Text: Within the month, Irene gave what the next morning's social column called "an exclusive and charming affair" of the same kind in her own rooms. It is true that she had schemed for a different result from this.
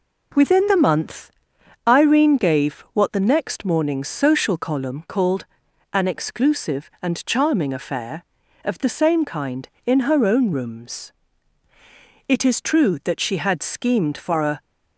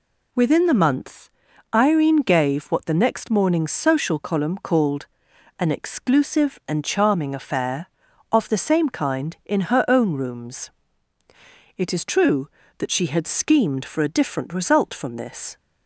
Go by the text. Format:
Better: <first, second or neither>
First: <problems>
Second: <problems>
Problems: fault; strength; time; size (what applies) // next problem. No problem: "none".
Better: second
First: pauses between "called" and "an"; noticeable; at 5.4 s; 0.48 s long // stops before "different result from this"; at 14.5 s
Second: pauses between "called" and "an"; noticeable; at 5.0 s; 0.52 s long